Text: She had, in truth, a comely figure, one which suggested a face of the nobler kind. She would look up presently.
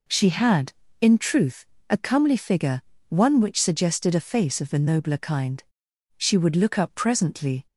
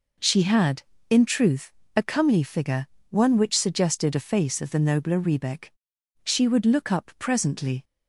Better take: first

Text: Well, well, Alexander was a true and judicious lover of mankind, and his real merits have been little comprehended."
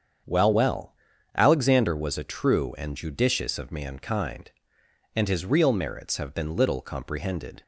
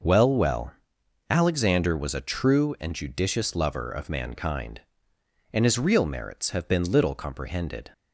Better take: second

